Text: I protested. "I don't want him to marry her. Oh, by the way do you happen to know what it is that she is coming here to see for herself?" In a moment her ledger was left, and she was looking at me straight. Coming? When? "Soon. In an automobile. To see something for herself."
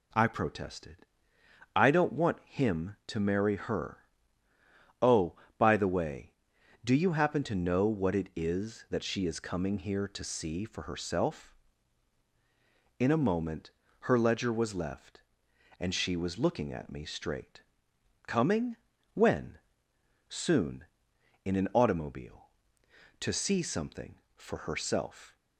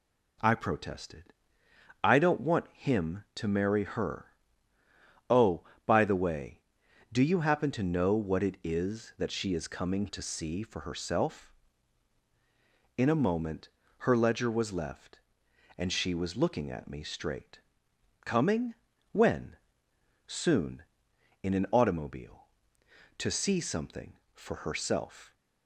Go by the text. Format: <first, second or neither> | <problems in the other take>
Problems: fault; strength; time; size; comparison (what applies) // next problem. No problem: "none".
first | skips "here"; at 10.0 s // pauses between "moment" and "her"; at 13.6 s; 0.38 s long; also in the first